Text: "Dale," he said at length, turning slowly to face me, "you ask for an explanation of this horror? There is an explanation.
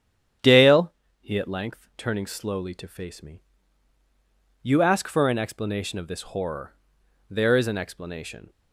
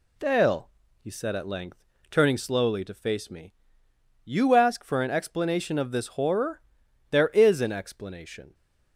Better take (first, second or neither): second